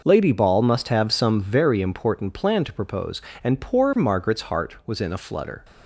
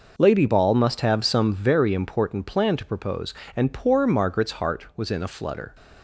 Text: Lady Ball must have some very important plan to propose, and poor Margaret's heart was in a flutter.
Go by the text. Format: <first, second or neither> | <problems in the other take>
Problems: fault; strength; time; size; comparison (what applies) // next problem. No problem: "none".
neither | none